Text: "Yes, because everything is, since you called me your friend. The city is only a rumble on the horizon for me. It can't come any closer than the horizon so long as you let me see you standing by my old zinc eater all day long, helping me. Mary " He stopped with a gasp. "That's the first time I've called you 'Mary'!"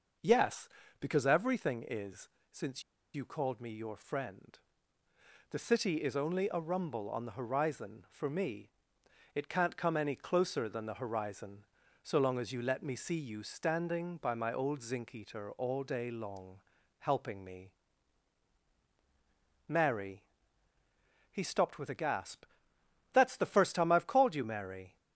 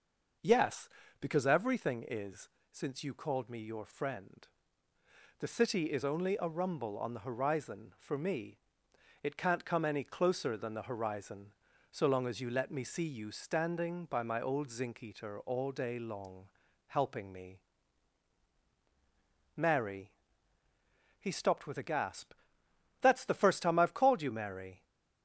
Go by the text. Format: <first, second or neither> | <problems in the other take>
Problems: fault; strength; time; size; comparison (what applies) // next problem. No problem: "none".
second | pauses between "since" and "you"; slight; at 2.8 s; 0.31 s long